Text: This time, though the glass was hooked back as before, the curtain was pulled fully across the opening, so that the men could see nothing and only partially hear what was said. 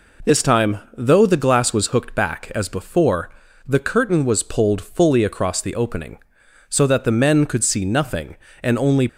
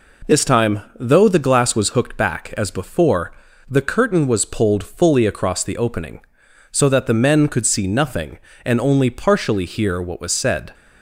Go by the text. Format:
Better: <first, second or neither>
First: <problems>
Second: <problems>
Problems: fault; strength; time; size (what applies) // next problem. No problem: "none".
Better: second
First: stops before "partially hear what was said"; at 9.0 s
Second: none